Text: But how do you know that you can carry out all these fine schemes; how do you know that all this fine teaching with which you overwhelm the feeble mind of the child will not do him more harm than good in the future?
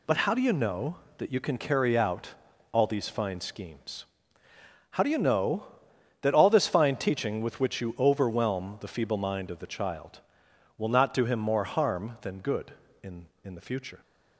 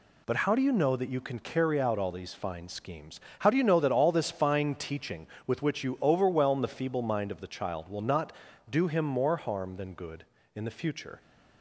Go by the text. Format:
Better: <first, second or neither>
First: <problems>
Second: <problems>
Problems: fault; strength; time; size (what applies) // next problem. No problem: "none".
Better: second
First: pauses between "out" and "all"; at 2.3 s; 0.42 s long // says "in" twice; at 13.4 s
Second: none